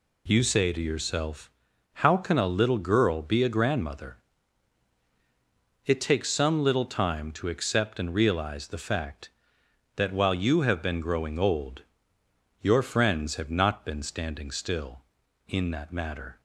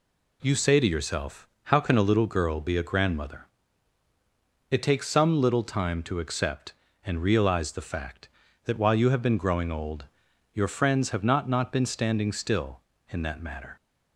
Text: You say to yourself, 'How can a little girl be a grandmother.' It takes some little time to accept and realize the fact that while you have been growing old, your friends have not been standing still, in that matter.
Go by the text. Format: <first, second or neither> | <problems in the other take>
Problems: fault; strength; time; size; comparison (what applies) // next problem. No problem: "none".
first | says "not" twice; at 11.4 s